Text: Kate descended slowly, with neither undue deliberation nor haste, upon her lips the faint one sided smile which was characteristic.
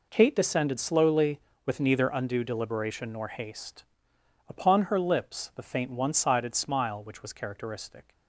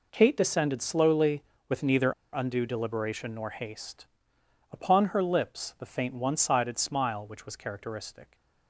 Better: first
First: none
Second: pauses between "neither" and "undue"; slight; at 2.1 s; 0.21 s long

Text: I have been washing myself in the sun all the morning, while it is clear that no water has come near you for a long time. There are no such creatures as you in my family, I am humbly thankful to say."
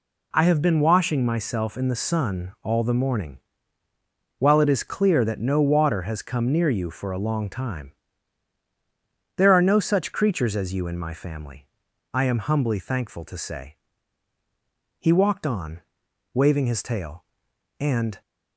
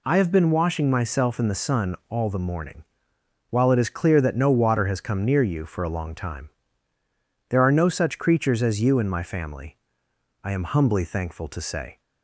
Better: second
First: goes on to say "He walked on waving his tail and"; strong; from 14.9 s on; 3.2 s long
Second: none

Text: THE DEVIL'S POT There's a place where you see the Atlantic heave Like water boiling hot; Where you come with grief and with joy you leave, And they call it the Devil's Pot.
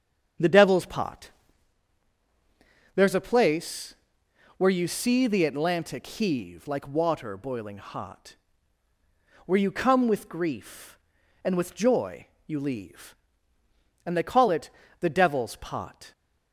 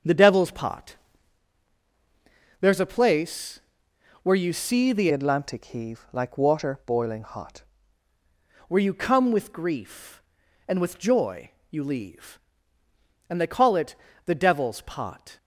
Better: first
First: starts louder than the rest; strong; until 3.0 s; 8 dB // pauses between "POT" and "There's"; strong; at 1.3 s; 1.6 s long // pauses between "place" and "where"; noticeable; at 3.9 s; 0.62 s long // pauses between "joy" and "you"; slight; at 12.2 s; 0.18 s long // pauses between "it" and "the"; slight; at 14.6 s; 0.30 s long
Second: starts louder than the rest; strong; until 2.6 s; 7.5 dB // pauses between "POT" and "There's"; strong; at 0.9 s; 1.6 s long // pauses between "place" and "where"; noticeable; at 3.6 s; 0.62 s long // changes voice from "Atlantic" to "hot"; from 5.1 to 7.6 s; 2.5 s long // pauses between "joy" and "you"; slight; at 11.5 s; 0.18 s long // pauses between "it" and "the"; slight; at 13.9 s; 0.30 s long

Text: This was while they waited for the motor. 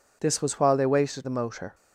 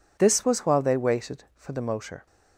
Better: second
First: skips "for"; at 1.2 s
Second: none

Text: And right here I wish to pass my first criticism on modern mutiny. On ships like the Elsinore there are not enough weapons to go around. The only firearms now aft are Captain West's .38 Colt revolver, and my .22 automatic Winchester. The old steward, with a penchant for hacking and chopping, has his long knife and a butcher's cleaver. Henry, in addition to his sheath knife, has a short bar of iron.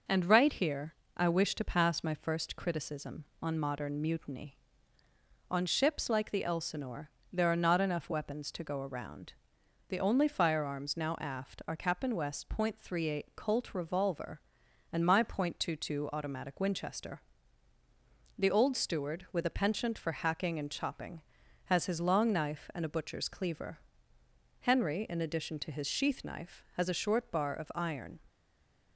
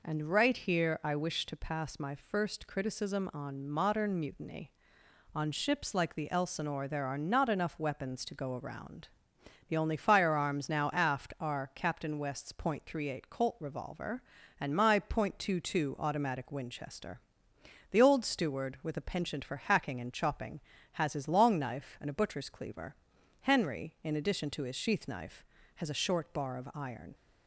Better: second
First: pauses between "here" and "I"; slight; at 0.9 s; 0.24 s long // pauses between "Elsinore" and "there"; slight; at 7.0 s; 0.24 s long // stays silent after the last word; slight; from 28.2 s on; 0.7 s long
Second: none

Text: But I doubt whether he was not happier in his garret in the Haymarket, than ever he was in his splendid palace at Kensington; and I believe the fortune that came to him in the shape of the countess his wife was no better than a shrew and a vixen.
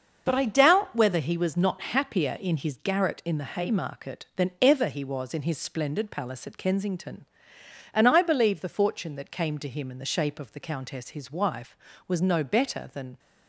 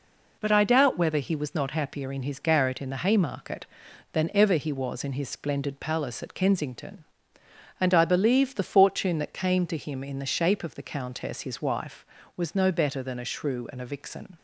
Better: second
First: starts louder than the rest; until 1.2 s; 6.5 dB // stops before "a shrew and a vixen"; at 13.1 s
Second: none

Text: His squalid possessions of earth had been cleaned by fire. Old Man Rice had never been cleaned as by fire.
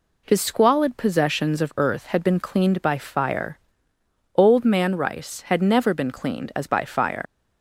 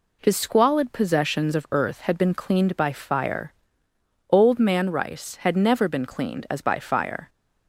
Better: second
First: leaves "fire" unfinished; at 7.2 s; 90 ms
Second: none

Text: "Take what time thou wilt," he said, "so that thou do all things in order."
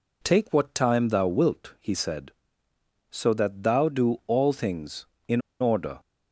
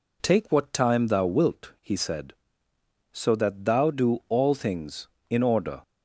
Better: second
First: pauses between "in" and "order"; slight; at 5.4 s; 0.20 s long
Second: none

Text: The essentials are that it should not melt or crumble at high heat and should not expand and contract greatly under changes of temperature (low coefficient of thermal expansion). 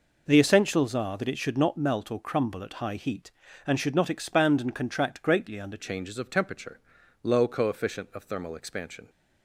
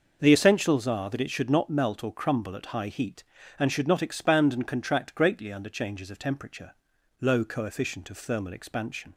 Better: second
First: changes voice at "changes"; from 5.7 s on; 3.3 s long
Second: none

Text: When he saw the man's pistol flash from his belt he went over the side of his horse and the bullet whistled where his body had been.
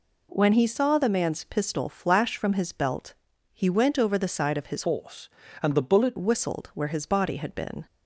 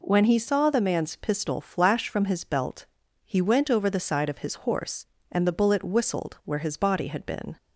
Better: second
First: pauses between "belt" and "he"; at 3.1 s; 0.38 s long // changes voice from "horse" to "bullet"; from 4.8 to 6.1 s; 1.3 s long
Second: pauses between "belt" and "he"; at 2.8 s; 0.38 s long

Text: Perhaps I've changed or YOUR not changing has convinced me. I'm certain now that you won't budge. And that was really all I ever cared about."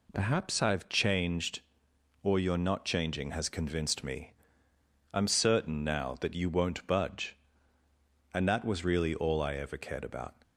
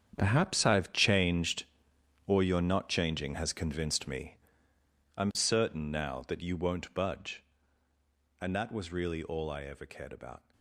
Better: first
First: none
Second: gets quieter; strong; throughout; 15 dB

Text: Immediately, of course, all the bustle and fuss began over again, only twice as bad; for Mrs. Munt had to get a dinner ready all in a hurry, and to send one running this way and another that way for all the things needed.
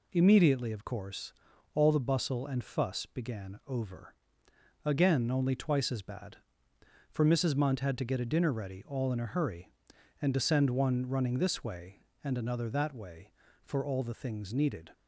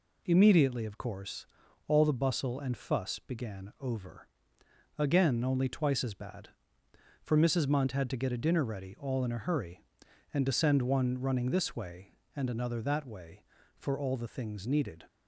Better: neither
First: pauses between "over" and "again"; noticeable; at 4.1 s; 0.72 s long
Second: pauses between "over" and "again"; noticeable; at 4.2 s; 0.72 s long

